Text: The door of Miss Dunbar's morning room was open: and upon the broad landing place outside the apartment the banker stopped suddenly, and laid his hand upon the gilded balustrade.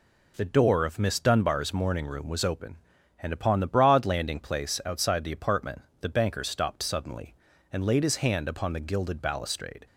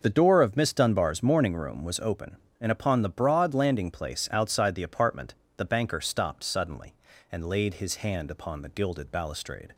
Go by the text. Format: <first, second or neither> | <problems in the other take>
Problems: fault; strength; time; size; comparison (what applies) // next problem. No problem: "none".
neither | pauses between "apartment" and "the"; slight; the same in both